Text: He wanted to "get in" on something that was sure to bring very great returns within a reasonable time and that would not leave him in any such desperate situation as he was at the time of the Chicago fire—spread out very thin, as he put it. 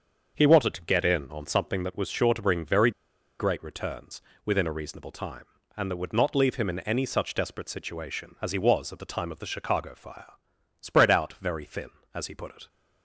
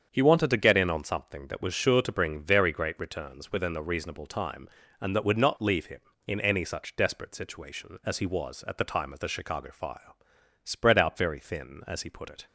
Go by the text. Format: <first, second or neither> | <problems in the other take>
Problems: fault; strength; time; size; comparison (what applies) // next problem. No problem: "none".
second | starts louder than the rest; until 1.3 s; 6.5 dB; strong in the second // pauses between "very" and "great"; noticeable; at 2.8 s; 0.49 s long // pauses between "returns" and "within"; slight; at 4.2 s; 0.24 s long